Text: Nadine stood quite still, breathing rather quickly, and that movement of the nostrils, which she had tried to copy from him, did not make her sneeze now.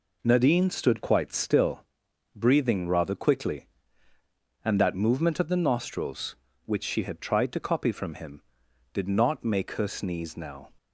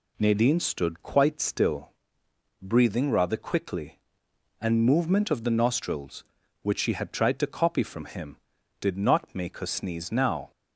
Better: first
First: none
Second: skips "that"; at 4.8 s

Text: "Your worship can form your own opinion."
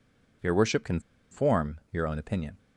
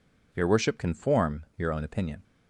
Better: second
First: pauses between "can" and "form"; slight; at 1.0 s; 0.30 s long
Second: none

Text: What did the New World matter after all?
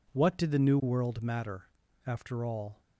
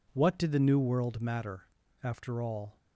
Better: neither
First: pauses between "matter" and "after"; slight; at 1.6 s; 0.36 s long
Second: pauses between "matter" and "after"; slight; at 1.6 s; 0.34 s long

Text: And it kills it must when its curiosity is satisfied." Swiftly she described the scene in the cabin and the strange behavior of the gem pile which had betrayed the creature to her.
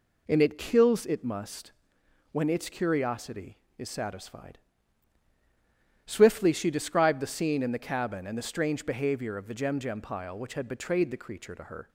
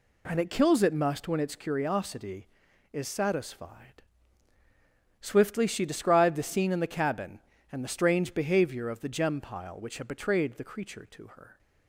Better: second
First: pauses between "must" and "when"; noticeable; at 1.7 s; 0.60 s long // says "gem" twice; at 9.7 s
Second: none

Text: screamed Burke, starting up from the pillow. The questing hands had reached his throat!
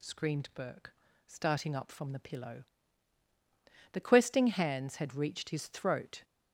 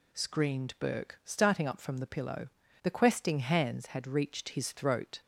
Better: neither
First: none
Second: none

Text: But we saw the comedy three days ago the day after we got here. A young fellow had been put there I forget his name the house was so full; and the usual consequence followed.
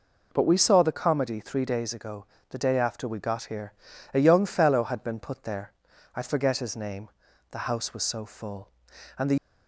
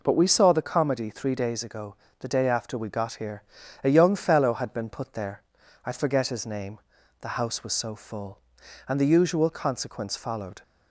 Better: second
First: pauses between "ago" and "the"; slight; at 2.2 s; 0.24 s long // pauses between "there" and "I"; at 5.7 s; 0.44 s long // pauses between "name" and "the"; at 7.0 s; 0.42 s long // stops before "usual consequence followed"; at 9.3 s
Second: pauses between "ago" and "the"; slight; at 1.9 s; 0.24 s long // pauses between "there" and "I"; at 5.4 s; 0.44 s long // pauses between "name" and "the"; at 6.7 s; 0.42 s long

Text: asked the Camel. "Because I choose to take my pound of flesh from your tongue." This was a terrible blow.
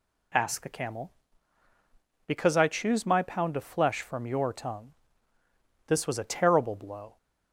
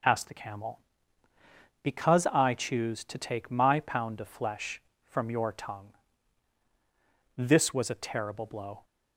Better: second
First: skips "to take"; at 3.0 s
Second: none

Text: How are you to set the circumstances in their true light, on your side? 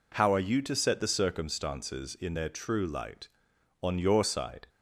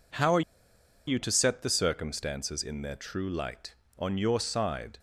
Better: first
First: none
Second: pauses between "are" and "you"; noticeable; at 0.4 s; 0.66 s long

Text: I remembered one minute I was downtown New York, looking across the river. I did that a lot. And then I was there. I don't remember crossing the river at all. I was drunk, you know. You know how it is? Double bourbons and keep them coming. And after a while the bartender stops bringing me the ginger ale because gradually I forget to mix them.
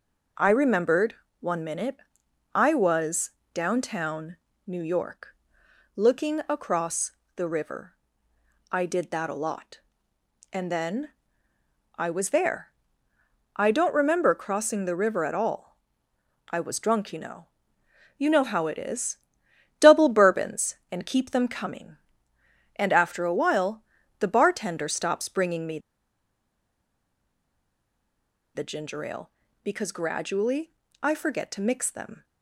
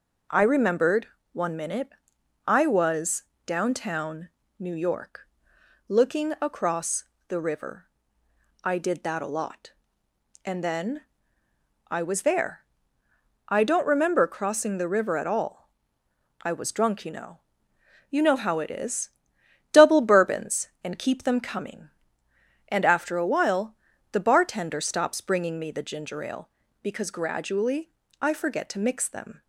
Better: second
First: pauses between "remembered" and "one"; slight; at 1.1 s; 0.26 s long // pauses between "minute" and "I"; noticeable; at 1.9 s; 0.58 s long // pauses between "was" and "downtown"; slight; at 3.3 s; 0.22 s long // pauses between "downtown" and "New"; slight; at 4.3 s; 0.30 s long // pauses between "across" and "the"; slight; at 7.1 s; 0.24 s long // pauses between "then" and "I"; noticeable; at 11.0 s; 0.90 s long // pauses between "while" and "the"; slight; at 23.8 s; 0.36 s long // pauses between "me" and "the"; strong; at 25.7 s; 2.7 s long // pauses between "gradually" and "I"; slight; at 30.7 s; 0.32 s long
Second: pauses between "remembered" and "one"; slight; at 1.0 s; 0.26 s long // pauses between "minute" and "I"; noticeable; at 1.8 s; 0.58 s long // pauses between "was" and "downtown"; slight; at 3.2 s; 0.22 s long // pauses between "downtown" and "New"; slight; at 4.2 s; 0.30 s long // pauses between "across" and "the"; slight; at 7.0 s; 0.24 s long // pauses between "then" and "I"; noticeable; at 11.0 s; 0.90 s long // pauses between "while" and "the"; slight; at 23.7 s; 0.36 s long // pauses between "gradually" and "I"; slight; at 27.9 s; 0.32 s long

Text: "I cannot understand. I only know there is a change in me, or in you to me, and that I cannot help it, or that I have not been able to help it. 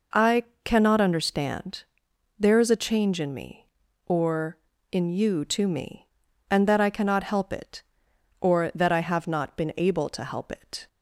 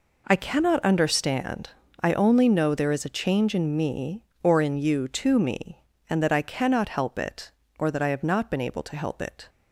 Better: second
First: pauses between "I" and "cannot"; slight; at 0.4 s; 0.22 s long // skips "I only know"; at 2.0 s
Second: none

